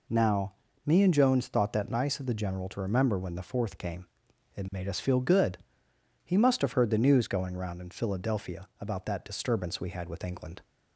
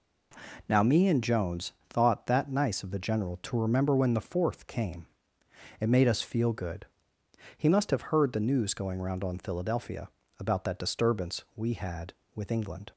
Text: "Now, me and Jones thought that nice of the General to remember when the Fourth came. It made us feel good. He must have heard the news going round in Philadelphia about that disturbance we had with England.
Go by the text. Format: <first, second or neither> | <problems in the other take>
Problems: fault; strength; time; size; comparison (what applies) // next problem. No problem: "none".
first | pauses between "Jones" and "thought"; slight; at 1.7 s; 0.18 s long // says "on" for "in"; at 9.2 s // pauses between "Philadelphia" and "about"; slight; at 10.0 s; 0.30 s long